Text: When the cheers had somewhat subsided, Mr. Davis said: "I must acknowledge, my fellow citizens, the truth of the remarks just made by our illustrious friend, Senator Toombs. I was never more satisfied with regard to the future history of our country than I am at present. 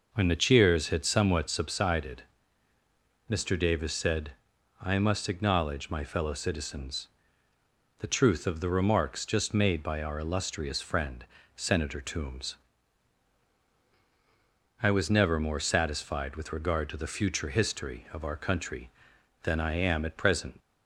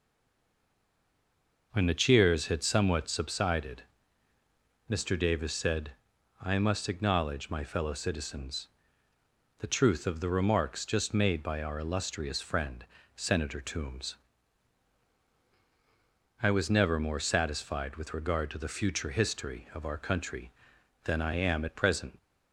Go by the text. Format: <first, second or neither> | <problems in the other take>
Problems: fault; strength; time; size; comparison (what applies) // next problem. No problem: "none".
first | stays silent before the first word; noticeable; until 1.7 s; 1.7 s long